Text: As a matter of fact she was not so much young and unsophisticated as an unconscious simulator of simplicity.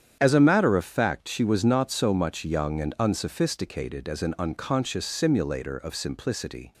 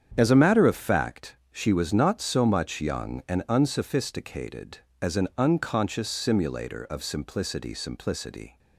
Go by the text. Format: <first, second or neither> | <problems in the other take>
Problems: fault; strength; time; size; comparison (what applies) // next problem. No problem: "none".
first | starts louder than the rest; strong; until 1.1 s; 8.5 dB; strong in the first // says "simplicity" twice; at 7.7 s